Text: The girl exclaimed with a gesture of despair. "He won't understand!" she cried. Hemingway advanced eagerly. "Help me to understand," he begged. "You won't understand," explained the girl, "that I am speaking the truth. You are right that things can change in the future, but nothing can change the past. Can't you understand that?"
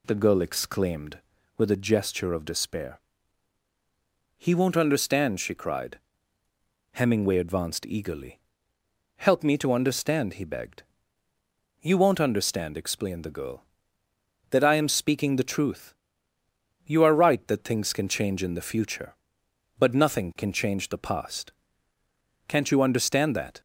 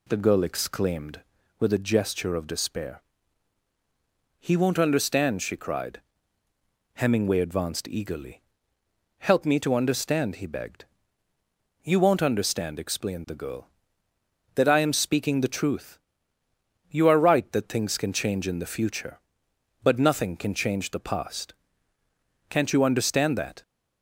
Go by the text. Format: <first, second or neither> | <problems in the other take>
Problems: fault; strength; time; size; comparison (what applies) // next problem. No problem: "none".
neither | none